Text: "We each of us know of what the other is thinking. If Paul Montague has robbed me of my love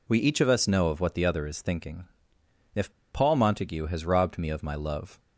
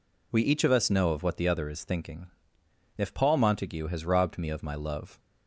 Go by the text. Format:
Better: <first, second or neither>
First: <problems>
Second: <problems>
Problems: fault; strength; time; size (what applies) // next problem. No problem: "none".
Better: second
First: pauses between "If" and "Paul"; slight; at 2.9 s; 0.22 s long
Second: none